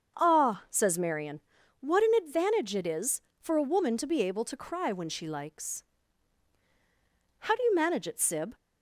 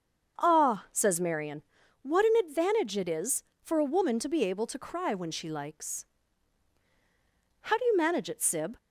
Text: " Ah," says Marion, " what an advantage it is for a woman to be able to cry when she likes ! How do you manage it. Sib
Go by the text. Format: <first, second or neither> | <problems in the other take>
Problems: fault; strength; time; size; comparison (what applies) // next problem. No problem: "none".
neither | starts louder than the rest; the same in both